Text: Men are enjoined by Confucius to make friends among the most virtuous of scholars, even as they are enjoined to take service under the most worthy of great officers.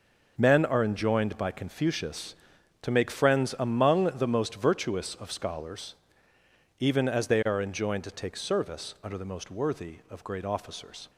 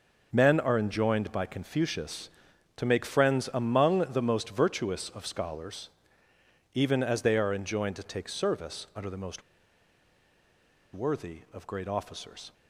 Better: first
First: none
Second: pauses between "most" and "worthy"; strong; at 9.4 s; 1.5 s long

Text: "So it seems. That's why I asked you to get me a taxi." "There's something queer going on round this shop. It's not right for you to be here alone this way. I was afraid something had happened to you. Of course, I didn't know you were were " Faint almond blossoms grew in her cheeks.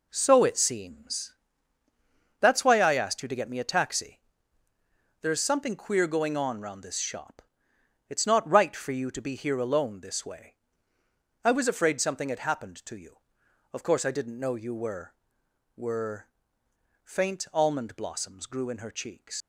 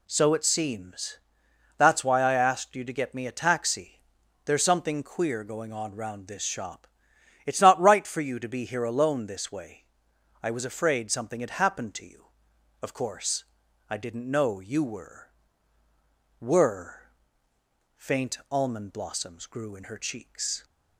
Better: second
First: leaves "cheeks" unfinished; at 19.4 s; 85 ms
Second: none

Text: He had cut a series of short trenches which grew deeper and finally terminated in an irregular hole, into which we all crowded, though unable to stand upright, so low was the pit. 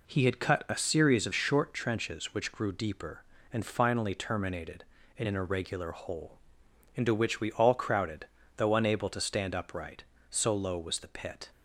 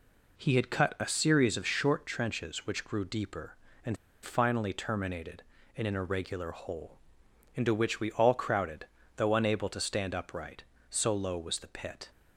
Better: first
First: none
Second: pauses between "and" and "finally"; slight; at 3.9 s; 0.26 s long

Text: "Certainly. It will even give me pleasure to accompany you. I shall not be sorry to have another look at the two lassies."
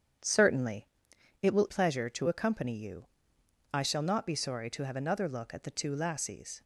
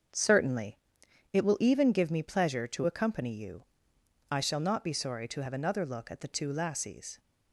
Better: second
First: starts louder than the rest; strong; until 1.7 s; 8 dB // skips "even give me"; at 1.6 s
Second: starts louder than the rest; until 1.6 s; 6.5 dB

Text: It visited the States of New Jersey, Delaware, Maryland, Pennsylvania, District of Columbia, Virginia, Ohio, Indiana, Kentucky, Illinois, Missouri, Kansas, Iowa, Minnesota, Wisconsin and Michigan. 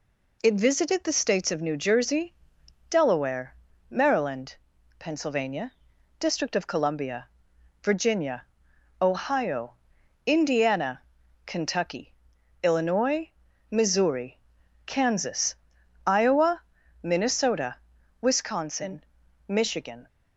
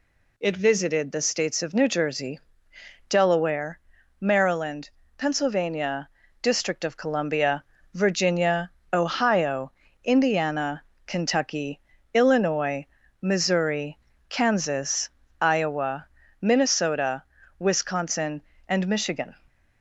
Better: second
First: skips "and"; at 19.2 s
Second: none

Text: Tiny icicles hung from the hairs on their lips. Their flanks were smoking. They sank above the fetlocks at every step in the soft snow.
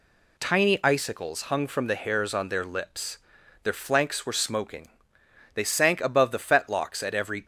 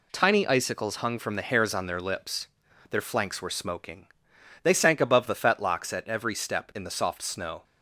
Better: second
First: stops before "step in the soft snow"; at 7.4 s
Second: none

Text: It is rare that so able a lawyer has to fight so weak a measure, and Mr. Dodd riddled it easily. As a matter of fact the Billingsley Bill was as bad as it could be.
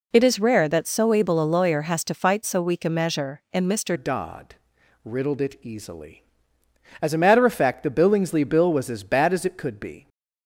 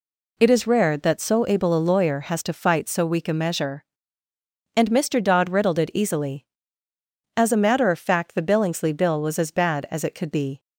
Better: second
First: changes voice at "Dodd"; from 3.9 s on; 6.1 s long // pauses between "Dodd" and "riddled"; noticeable; at 4.5 s; 0.50 s long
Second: none

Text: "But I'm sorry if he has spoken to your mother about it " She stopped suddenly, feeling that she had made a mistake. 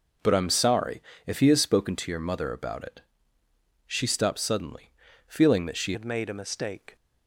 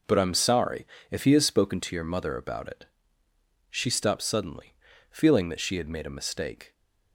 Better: second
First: pauses between "sorry" and "if"; slight; at 1.0 s; 0.24 s long // changes voice at "had"; from 5.9 s on; 1.0 s long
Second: pauses between "sorry" and "if"; slight; at 0.8 s; 0.24 s long

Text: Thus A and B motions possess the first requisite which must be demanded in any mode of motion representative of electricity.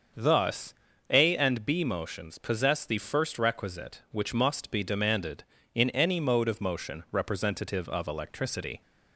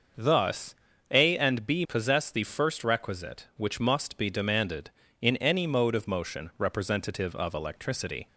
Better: first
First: starts louder than the rest; until 1.5 s; 6.5 dB // pauses between "Thus" and "A"; slight; at 0.7 s; 0.36 s long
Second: starts louder than the rest; until 1.5 s; 6 dB // pauses between "Thus" and "A"; slight; at 0.7 s; 0.36 s long // skips "motions"; at 1.8 s

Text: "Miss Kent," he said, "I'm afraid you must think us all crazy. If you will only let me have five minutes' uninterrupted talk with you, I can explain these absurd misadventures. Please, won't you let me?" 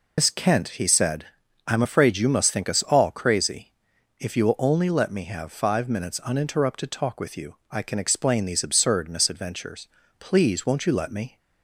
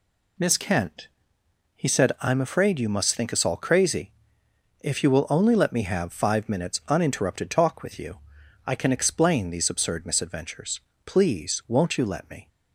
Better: second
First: loses the start of "Miss"; at 0.1 s; 95 ms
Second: none

